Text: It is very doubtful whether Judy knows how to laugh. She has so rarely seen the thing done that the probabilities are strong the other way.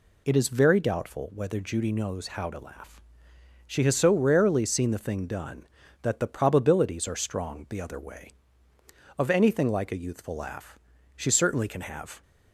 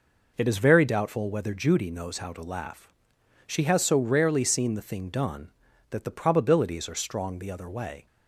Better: second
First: goes on to say "Of anything like a youthful laugh she certainly can have"; strong; from 9.1 s on; 3.0 s long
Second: none

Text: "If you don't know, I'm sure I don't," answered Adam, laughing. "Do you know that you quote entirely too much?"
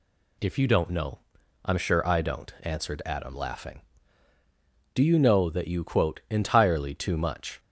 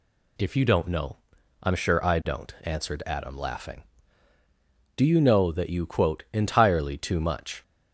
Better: neither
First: none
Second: none

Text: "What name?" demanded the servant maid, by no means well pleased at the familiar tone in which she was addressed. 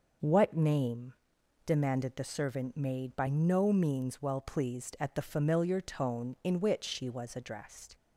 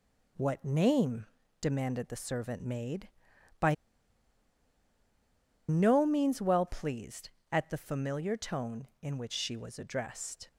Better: first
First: none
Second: pauses between "by" and "no"; strong; at 3.7 s; 1.9 s long

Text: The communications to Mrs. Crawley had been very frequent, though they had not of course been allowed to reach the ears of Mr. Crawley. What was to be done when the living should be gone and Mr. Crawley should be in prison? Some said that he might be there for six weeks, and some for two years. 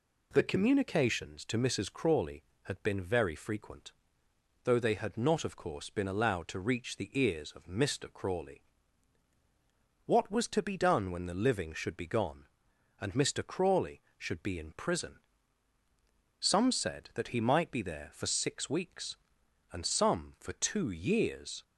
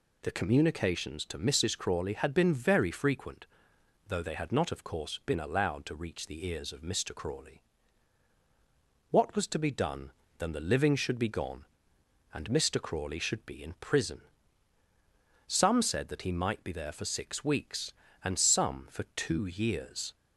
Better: first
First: none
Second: says "then" for "when"; at 10.3 s

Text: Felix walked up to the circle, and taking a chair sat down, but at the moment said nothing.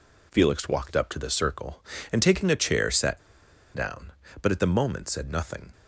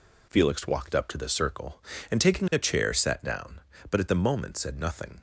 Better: second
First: pauses between "sat" and "down"; noticeable; at 3.1 s; 0.54 s long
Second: none

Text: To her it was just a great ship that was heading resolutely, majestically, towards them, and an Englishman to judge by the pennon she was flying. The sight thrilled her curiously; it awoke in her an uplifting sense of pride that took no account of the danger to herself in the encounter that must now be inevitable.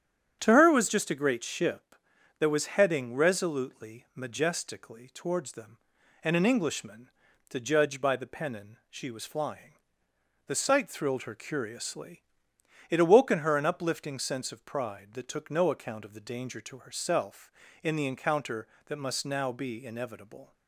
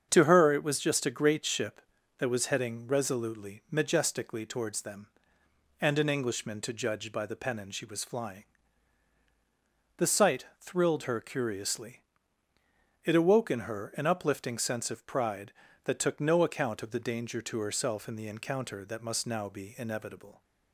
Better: neither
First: starts louder than the rest; strong; until 1.4 s; 8.5 dB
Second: starts louder than the rest; strong; until 1.1 s; 7 dB

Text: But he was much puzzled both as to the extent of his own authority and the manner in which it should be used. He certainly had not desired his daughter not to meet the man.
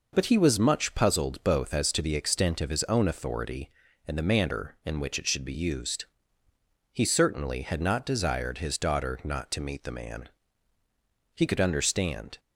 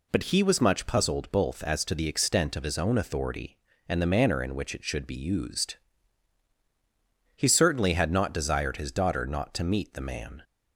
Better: second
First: goes on to say "He could understand"; noticeable; from 11.3 s on; 1.0 s long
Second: none

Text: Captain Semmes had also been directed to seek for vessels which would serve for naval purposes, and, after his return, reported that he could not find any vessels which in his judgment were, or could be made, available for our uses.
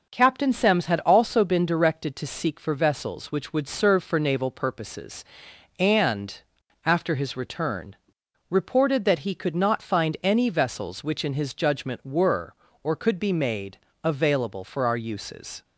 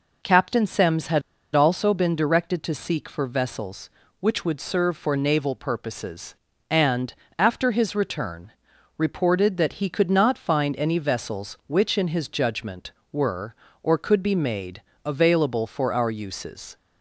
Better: first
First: none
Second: pauses between "had" and "also"; slight; at 1.2 s; 0.33 s long

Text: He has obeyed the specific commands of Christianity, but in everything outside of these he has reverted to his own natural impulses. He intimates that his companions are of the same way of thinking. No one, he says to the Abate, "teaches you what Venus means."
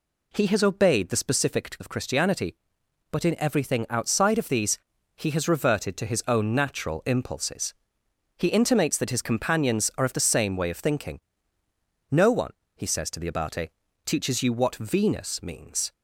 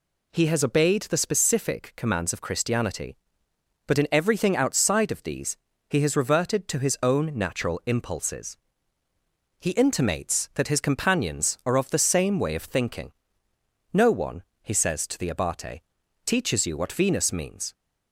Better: second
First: skips "commands"; at 1.7 s // pauses between "these" and "he"; at 4.7 s; 0.38 s long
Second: pauses between "these" and "he"; slight; at 5.5 s; 0.32 s long

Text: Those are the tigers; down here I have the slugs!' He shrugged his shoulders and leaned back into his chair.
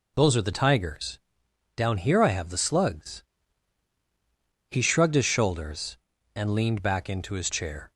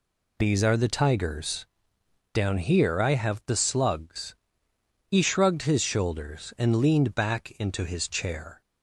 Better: first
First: none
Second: says "These" for "Those"; at 0.3 s

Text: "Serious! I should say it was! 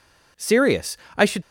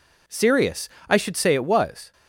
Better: second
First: stops before "say it was"; at 1.4 s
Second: none

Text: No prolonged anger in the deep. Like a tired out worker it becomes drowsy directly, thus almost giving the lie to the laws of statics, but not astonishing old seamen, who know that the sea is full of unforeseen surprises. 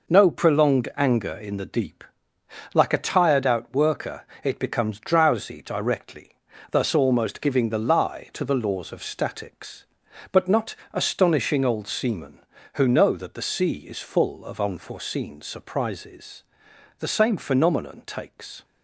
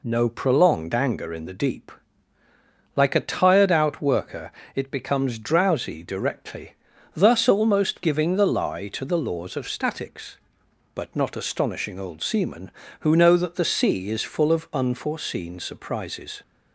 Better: second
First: pauses between "worker" and "it"; slight; at 4.2 s; 0.18 s long // pauses between "not" and "astonishing"; slight; at 10.7 s; 0.18 s long // goes on to say "The same phenomenon takes"; from 16.9 s on; 1.6 s long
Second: pauses between "worker" and "it"; slight; at 4.5 s; 0.22 s long

